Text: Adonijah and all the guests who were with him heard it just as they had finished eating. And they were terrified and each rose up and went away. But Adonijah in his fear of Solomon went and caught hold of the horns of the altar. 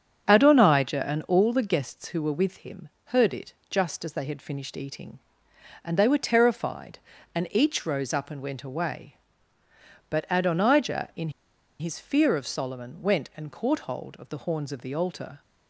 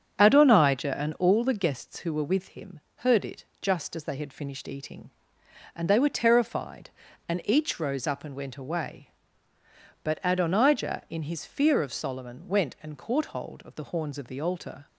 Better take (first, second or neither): second